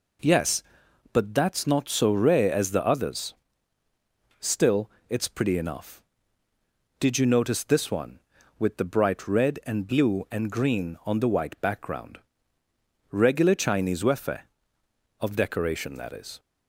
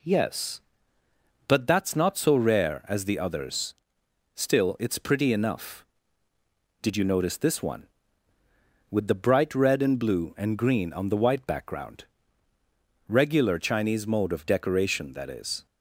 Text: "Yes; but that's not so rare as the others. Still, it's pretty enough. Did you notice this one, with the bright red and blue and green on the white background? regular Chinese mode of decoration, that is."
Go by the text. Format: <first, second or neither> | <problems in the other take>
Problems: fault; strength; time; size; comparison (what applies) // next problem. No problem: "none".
second | says "wefe" for "mode"; at 14.0 s